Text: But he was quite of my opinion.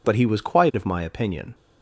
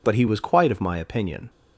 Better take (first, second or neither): neither